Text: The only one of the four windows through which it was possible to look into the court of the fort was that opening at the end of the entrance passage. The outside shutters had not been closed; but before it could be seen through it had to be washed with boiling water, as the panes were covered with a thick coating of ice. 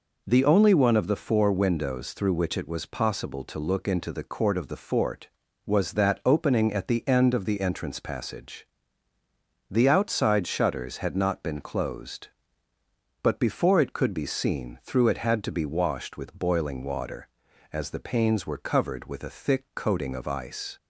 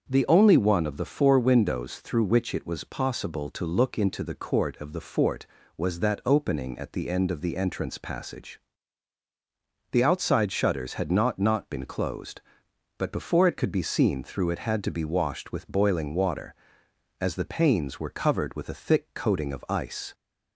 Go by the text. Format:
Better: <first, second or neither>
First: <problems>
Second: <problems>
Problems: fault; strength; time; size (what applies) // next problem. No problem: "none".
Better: first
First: none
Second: starts louder than the rest; until 1.1 s; 6.5 dB // says "not" twice; at 11.3 s